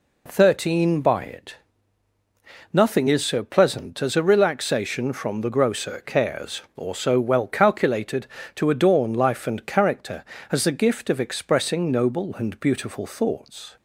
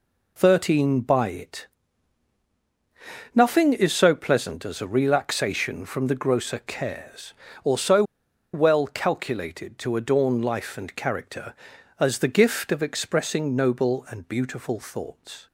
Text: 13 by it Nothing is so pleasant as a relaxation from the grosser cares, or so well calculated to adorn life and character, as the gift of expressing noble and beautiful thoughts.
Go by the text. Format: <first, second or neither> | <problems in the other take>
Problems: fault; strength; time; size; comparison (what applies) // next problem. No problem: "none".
first | pauses between "it" and "Nothing"; strong; at 1.6 s; 1.6 s long; also in the first // pauses between "so" and "well"; noticeable; at 8.0 s; 0.50 s long